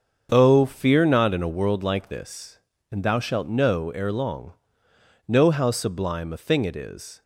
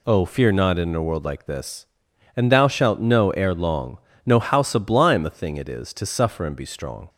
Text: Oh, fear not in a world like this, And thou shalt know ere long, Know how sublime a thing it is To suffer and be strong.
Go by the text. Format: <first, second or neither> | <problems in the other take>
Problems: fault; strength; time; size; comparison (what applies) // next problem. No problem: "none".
second | starts louder than the rest; until 1.3 s; 7 dB // stops before "To suffer and be strong"; at 7.2 s